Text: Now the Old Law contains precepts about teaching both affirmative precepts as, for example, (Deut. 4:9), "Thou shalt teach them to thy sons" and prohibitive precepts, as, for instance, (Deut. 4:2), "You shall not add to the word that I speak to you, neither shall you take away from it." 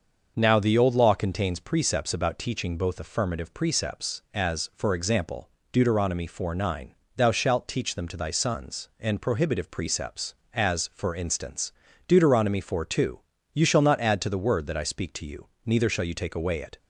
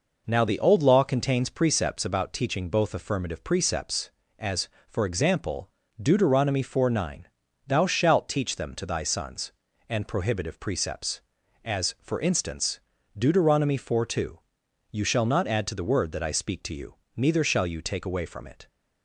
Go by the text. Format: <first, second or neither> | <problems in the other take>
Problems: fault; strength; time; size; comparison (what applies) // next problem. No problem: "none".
second | starts louder than the rest; until 1.3 s; 6 dB // skips "from"; at 16.5 s